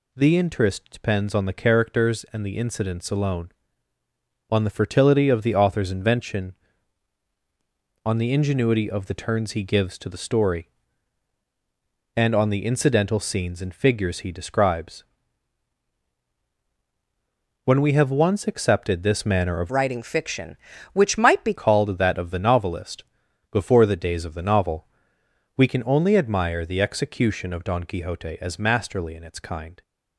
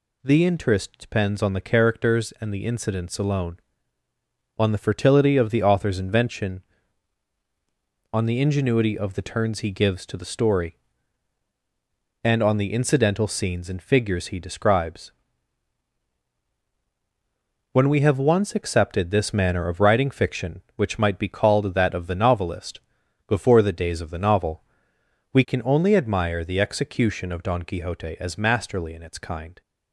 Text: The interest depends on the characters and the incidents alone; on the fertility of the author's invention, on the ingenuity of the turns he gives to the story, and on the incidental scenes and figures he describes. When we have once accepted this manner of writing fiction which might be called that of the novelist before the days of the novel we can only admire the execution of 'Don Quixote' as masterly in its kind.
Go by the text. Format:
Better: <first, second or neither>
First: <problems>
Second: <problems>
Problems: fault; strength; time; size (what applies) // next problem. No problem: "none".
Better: second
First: changes voice from "writing" to "be"; from 19.6 to 21.5 s; 1.9 s long // pauses between "novelist" and "before"; noticeable; at 23.0 s; 0.46 s long // pauses between "novel" and "we"; noticeable; at 24.8 s; 0.68 s long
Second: pauses between "novelist" and "before"; noticeable; at 22.7 s; 0.46 s long // pauses between "novel" and "we"; noticeable; at 24.6 s; 0.68 s long